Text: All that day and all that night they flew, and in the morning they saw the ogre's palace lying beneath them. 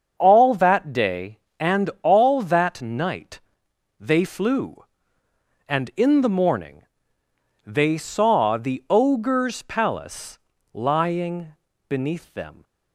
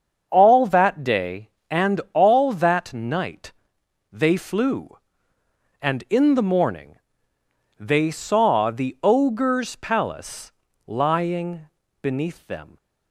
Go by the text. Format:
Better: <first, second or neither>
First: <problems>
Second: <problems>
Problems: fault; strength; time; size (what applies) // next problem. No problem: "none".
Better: neither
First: starts louder than the rest; until 1.1 s; 7 dB // pauses between "night" and "they"; noticeable; at 3.4 s; 0.60 s long // pauses between "morning" and "they"; noticeable; at 6.8 s; 0.82 s long // pauses between "palace" and "lying"; slight; at 10.3 s; 0.34 s long // pauses between "lying" and "beneath"; at 11.5 s; 0.38 s long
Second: starts louder than the rest; until 1.3 s; 7 dB // pauses between "night" and "they"; noticeable; at 3.5 s; 0.60 s long // pauses between "morning" and "they"; noticeable; at 6.9 s; 0.82 s long // pauses between "palace" and "lying"; slight; at 10.5 s; 0.34 s long // pauses between "lying" and "beneath"; at 11.6 s; 0.38 s long